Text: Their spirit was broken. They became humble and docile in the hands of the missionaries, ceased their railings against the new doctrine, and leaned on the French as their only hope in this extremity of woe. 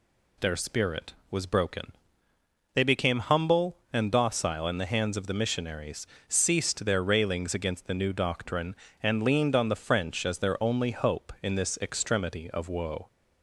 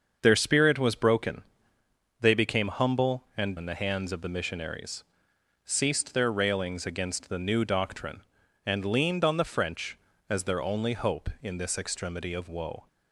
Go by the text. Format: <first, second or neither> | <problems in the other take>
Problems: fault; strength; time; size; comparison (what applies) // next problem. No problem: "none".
first | starts louder than the rest; until 1.2 s; 6.5 dB // skips "docile"; at 3.5 s